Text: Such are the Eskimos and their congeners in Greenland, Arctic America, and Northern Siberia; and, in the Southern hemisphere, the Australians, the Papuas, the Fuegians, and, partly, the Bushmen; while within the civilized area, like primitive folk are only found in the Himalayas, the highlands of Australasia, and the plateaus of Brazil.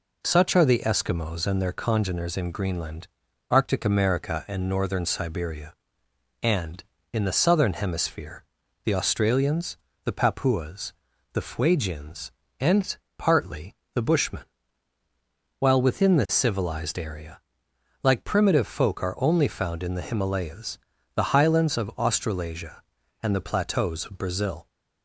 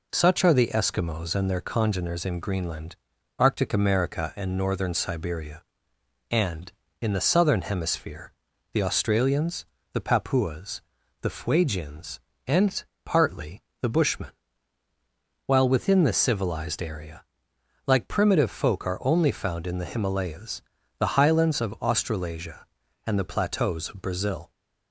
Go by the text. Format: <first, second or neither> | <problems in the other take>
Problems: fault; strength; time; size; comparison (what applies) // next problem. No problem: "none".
neither | none